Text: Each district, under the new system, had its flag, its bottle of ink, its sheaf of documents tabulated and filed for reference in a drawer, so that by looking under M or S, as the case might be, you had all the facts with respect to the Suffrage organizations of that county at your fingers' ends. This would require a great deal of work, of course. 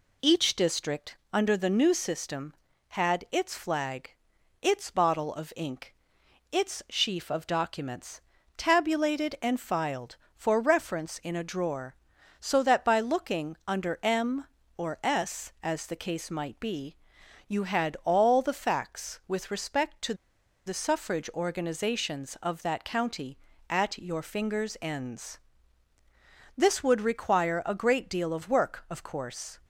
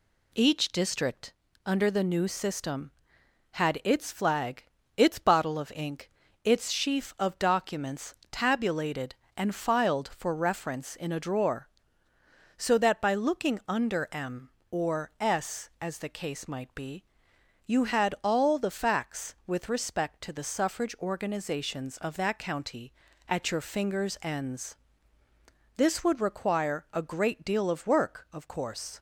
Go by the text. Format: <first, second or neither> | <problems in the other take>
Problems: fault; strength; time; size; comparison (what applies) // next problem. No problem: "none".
second | pauses between "documents" and "tabulated"; at 8.1 s; 0.38 s long; slight in the second // pauses between "to" and "the"; noticeable; at 20.1 s; 0.52 s long